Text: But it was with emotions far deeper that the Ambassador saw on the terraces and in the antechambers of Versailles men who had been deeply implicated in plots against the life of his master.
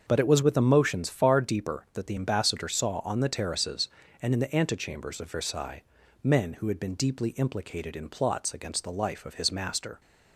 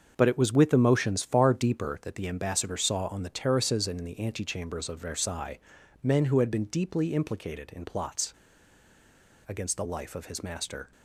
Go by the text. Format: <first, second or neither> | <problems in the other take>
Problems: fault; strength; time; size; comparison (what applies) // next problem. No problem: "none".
first | starts louder than the rest; until 1.1 s; 6.5 dB; also in the first // pauses between "Versailles" and "men"; noticeable; at 5.5 s; 0.46 s long; also in the first // pauses between "plots" and "against"; at 8.3 s; 1.1 s long